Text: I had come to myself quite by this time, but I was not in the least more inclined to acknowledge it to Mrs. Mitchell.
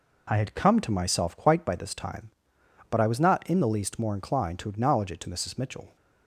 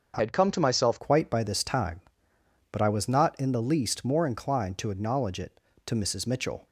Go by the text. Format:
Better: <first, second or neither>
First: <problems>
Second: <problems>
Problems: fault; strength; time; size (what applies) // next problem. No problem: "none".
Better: first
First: none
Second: starts louder than the rest; until 1.1 s; 6.5 dB // changes voice from "had" to "myself"; from 0.1 to 0.9 s; 0.8 s long